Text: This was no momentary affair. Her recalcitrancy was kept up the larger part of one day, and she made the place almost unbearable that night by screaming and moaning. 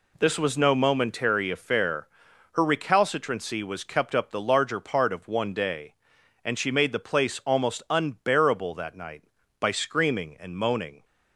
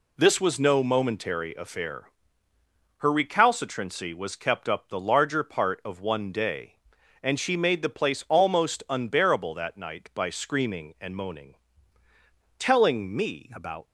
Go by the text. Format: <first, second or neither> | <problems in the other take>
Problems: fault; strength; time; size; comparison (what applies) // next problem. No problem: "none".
first | goes on to say "Telling me about"; noticeable; from 12.5 s on; 1.2 s long